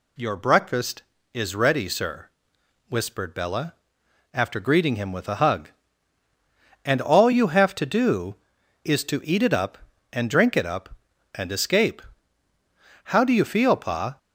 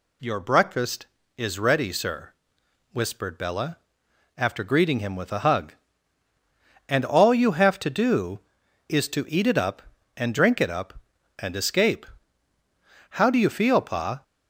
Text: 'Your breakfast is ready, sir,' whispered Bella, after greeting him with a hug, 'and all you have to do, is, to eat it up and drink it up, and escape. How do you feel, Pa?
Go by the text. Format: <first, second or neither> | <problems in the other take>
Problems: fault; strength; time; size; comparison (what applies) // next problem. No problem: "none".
neither | none